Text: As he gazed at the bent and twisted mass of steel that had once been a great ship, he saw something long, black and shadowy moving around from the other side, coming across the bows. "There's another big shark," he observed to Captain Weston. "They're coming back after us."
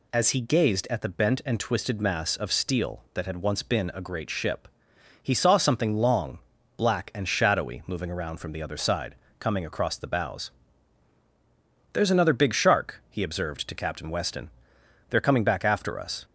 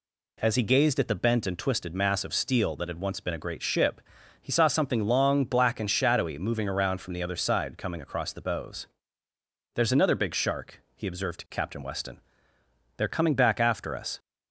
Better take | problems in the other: neither | none

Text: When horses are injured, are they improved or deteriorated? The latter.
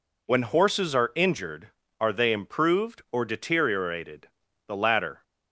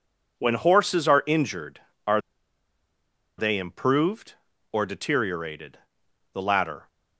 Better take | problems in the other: first | pauses between "are" and "they"; at 2.2 s; 1.1 s long

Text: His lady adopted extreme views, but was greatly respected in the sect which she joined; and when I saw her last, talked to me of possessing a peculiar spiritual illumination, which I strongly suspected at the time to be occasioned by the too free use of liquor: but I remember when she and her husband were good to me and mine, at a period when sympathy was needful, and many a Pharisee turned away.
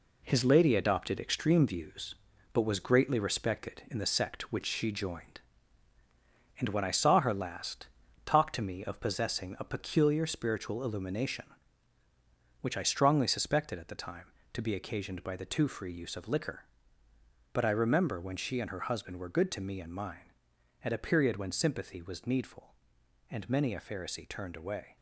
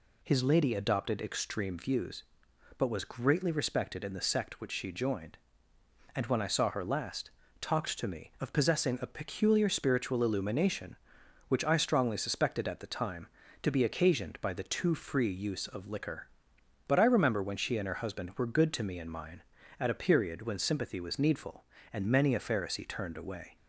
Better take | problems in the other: second | gets quieter; throughout; 6.5 dB

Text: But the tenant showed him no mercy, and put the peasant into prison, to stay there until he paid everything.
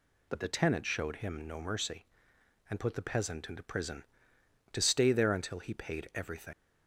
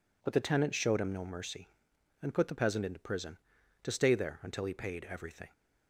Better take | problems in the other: second | leaves "everything" unfinished; at 6.5 s; 85 ms

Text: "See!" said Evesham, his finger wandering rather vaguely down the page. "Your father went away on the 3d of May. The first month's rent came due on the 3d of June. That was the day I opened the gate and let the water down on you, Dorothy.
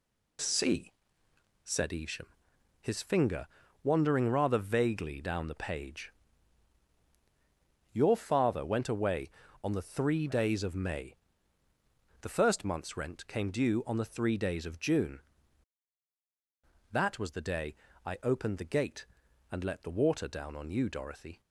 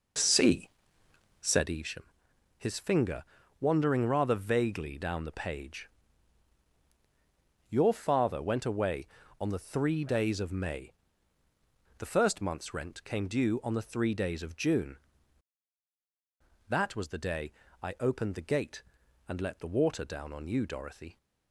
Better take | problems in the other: first | starts louder than the rest; noticeable; until 1.8 s; 5 dB // pauses between "finger" and "wandering"; at 3.2 s; 0.38 s long; also in the first // pauses between "day" and "I"; slight; at 17.5 s; 0.28 s long; slight in the first

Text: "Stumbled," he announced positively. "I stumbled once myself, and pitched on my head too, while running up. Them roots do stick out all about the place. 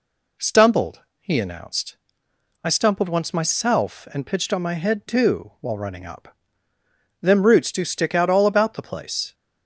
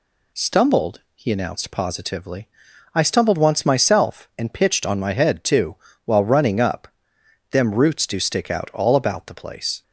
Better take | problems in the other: second | skips "positively"; at 2.2 s

